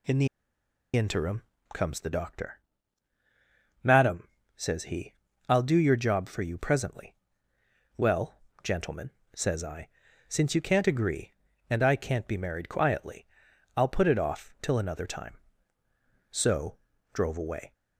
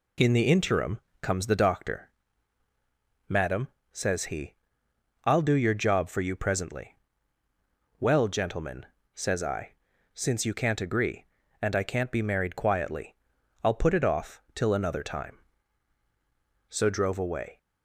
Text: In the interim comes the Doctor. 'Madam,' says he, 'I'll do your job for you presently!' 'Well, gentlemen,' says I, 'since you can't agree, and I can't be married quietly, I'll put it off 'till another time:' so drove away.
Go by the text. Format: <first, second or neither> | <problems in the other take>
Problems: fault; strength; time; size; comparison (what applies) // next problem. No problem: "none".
second | pauses between "the" and "interim"; noticeable; at 0.2 s; 0.68 s long // pauses between "interim" and "comes"; slight; at 1.4 s; 0.32 s long; slight in the second // pauses between "so" and "drove"; slight; at 16.7 s; 0.34 s long